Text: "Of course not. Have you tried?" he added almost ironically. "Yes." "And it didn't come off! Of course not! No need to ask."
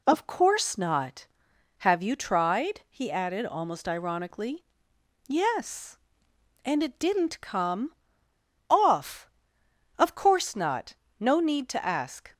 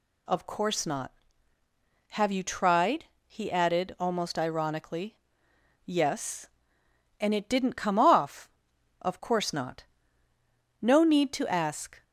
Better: second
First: pauses between "come" and "off"; noticeable; at 7.9 s; 0.77 s long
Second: none

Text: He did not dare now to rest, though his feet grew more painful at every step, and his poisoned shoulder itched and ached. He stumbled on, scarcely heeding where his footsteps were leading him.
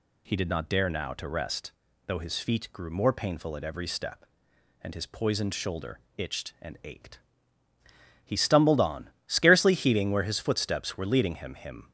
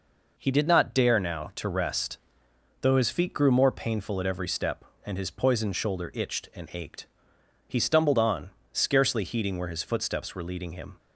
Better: second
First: pauses between "shoulder" and "itched"; slight; at 6.0 s; 0.18 s long // says "him" twice; at 11.5 s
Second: none

